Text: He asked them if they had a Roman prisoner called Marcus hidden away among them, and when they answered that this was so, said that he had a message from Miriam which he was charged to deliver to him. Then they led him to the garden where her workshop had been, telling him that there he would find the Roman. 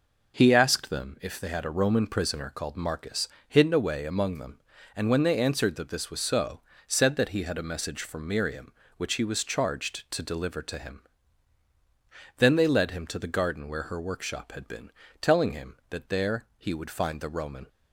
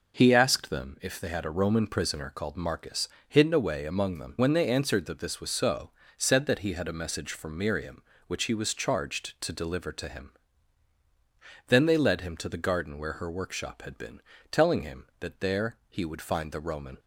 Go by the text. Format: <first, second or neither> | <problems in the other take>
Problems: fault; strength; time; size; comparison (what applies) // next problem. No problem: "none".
first | pauses between "Marcus" and "hidden"; slight; at 3.0 s; 0.18 s long; slight in the first // skips "and"; at 4.3 s